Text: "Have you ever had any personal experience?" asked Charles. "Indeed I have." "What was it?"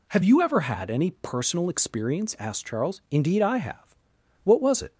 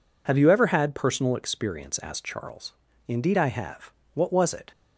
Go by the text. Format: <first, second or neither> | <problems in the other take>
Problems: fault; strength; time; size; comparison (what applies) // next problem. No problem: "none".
first | skips "any"; at 0.9 s